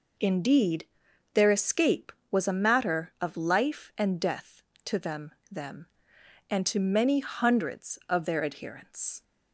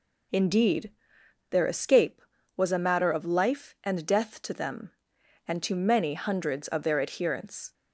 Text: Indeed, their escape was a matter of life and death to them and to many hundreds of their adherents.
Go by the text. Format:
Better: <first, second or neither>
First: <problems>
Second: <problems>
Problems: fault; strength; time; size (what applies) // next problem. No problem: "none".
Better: second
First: says "them" twice; at 5.5 s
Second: none